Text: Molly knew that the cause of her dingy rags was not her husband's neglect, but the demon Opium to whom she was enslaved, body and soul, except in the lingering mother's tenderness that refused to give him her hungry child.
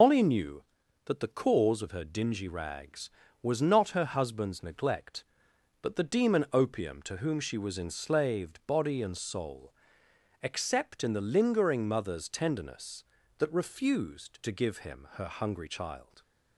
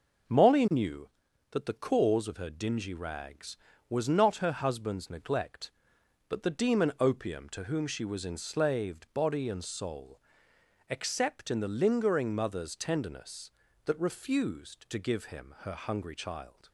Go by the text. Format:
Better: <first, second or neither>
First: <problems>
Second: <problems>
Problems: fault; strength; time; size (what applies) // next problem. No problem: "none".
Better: second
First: loses the start of "Molly"; at 0.0 s; 155 ms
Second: none